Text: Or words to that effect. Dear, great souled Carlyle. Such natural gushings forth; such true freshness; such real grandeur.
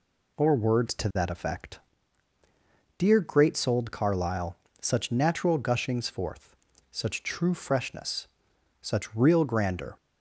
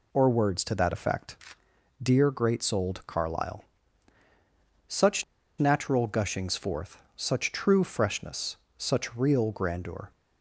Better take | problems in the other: first | pauses between "Such" and "natural"; slight; at 5.2 s; 0.34 s long

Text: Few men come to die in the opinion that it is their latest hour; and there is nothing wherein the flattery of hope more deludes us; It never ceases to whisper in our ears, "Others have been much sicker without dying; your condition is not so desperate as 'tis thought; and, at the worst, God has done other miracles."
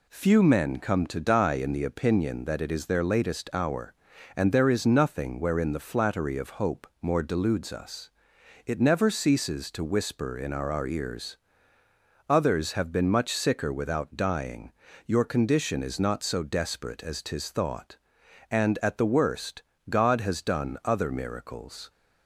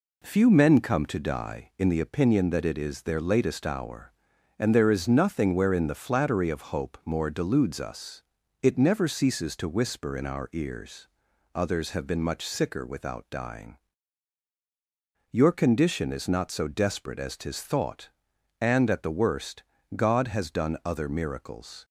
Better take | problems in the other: second | says "our" twice; at 10.7 s

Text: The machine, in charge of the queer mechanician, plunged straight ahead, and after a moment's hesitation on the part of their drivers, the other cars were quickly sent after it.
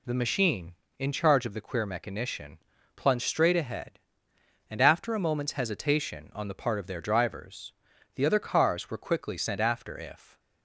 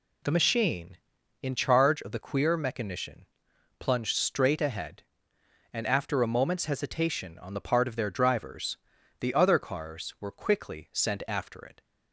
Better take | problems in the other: second | says "if" for "it"; at 9.9 s

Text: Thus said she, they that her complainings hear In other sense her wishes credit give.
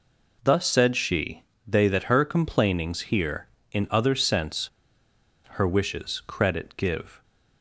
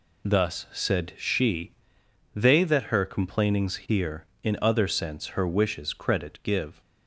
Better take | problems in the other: second | pauses between "sense" and "her"; noticeable; at 4.6 s; 0.80 s long

